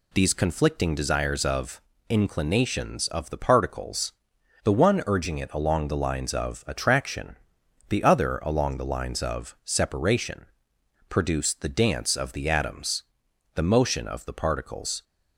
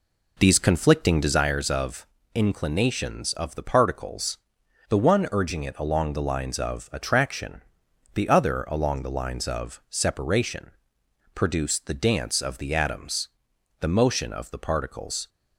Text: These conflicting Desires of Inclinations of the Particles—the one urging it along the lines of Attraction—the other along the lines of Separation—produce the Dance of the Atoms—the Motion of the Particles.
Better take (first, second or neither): first